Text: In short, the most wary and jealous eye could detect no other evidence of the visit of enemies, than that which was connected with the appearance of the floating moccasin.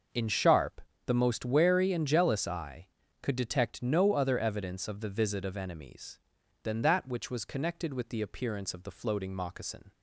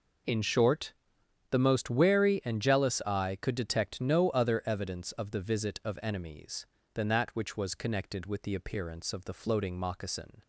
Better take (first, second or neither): second